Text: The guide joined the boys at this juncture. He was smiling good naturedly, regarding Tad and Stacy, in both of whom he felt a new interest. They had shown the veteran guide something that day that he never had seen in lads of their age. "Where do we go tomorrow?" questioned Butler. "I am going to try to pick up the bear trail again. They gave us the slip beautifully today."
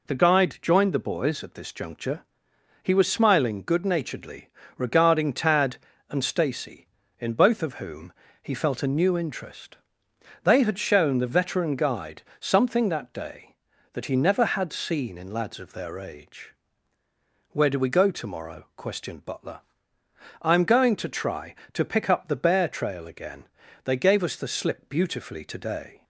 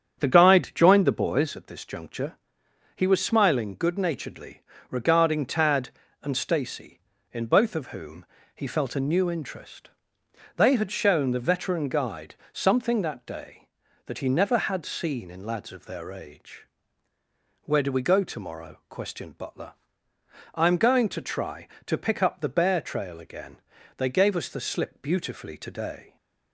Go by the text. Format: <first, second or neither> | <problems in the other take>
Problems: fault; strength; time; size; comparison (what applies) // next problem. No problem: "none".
first | starts louder than the rest; strong; until 1.6 s; 8 dB // pauses between "whom" and "he"; slight; at 8.2 s; 0.30 s long; slight in the first // pauses between "guide" and "something"; slight; at 12.3 s; 0.18 s long; slight in the first